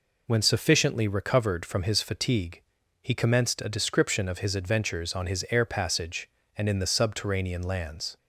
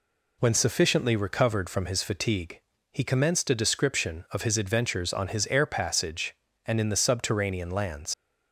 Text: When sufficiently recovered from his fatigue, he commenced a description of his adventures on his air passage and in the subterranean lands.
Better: first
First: none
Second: leaves "lands" unfinished; at 8.1 s; 85 ms

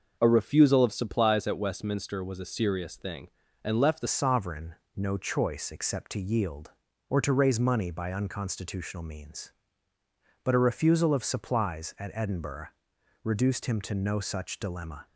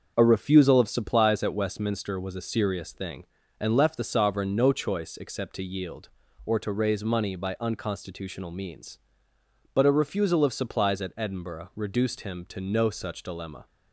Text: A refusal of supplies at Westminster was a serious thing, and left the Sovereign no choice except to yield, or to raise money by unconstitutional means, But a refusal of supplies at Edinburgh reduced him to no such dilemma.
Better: second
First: starts louder than the rest; noticeable; until 1.2 s; 6 dB // changes voice at "Sovereign"; from 4.0 s on; 11.0 s long // pauses between "Sovereign" and "no"; slight; at 4.7 s; 0.22 s long // pauses between "Edinburgh" and "reduced"; noticeable; at 12.6 s; 0.54 s long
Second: starts louder than the rest; until 1.1 s; 6.5 dB

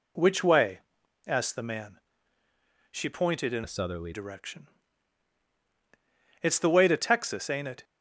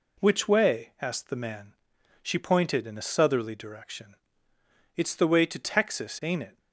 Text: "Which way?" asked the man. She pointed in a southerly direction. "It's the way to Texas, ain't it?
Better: second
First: changes voice from "a" to "southerly"; from 3.6 to 4.1 s; 0.5 s long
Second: none

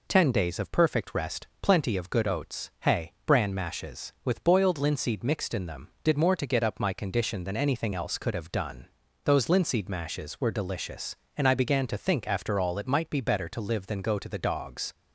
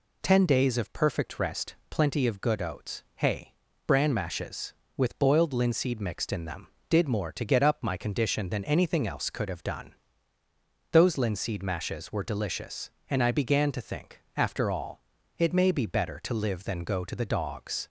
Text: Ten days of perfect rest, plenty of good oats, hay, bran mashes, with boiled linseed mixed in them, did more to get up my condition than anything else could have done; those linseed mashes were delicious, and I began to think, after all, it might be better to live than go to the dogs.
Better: first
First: none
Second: says "may" for "might"; at 15.5 s

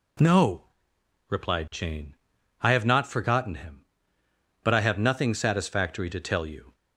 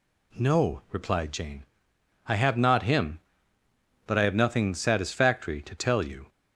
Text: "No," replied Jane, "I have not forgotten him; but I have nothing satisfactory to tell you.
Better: first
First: none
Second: skips "forgotten"; at 2.8 s

